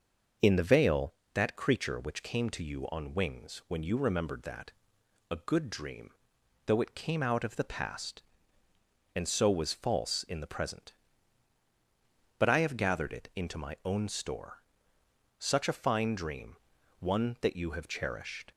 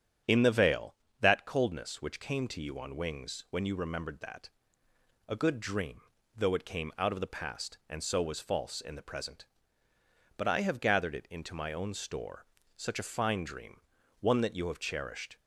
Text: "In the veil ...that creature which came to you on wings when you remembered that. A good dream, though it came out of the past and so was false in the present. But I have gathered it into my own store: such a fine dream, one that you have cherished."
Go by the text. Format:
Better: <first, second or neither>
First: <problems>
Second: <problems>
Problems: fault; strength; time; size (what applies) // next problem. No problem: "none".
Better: first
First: starts louder than the rest; noticeable; until 1.6 s; 6 dB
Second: starts louder than the rest; strong; until 1.4 s; 9 dB // says "coldness" for "creature"; at 1.4 s